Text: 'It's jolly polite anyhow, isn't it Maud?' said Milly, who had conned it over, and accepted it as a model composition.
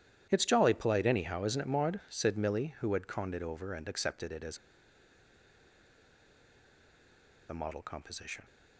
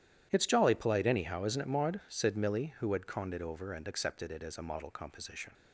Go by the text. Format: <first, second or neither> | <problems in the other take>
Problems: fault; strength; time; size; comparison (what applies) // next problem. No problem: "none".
second | starts louder than the rest; strong; until 1.3 s; 11 dB; strong in the second // pauses between "as" and "a"; strong; at 4.5 s; 2.9 s long